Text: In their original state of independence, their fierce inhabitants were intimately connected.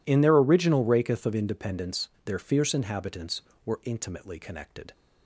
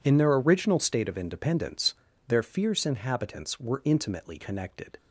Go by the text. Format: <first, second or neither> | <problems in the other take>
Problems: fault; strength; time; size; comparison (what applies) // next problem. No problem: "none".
second | says "raketh" for "state"; at 0.8 s